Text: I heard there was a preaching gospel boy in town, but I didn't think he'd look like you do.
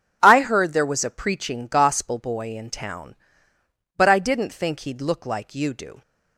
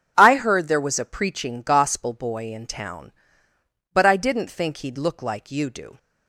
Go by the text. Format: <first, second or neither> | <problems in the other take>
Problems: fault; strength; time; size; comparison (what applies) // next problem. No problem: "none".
neither | none